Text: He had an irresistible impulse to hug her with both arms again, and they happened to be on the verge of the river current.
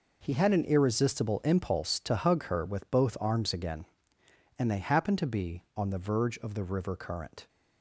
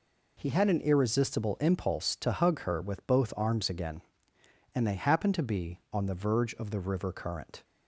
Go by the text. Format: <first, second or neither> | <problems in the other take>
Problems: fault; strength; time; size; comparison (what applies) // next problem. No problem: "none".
second | gets quieter; strong; throughout; 12 dB